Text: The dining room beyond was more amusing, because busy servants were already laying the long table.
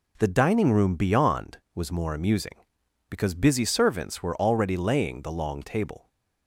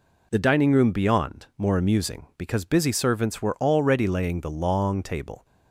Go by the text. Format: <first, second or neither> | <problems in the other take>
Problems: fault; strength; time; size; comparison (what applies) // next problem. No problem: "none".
first | skips "was"; at 1.5 s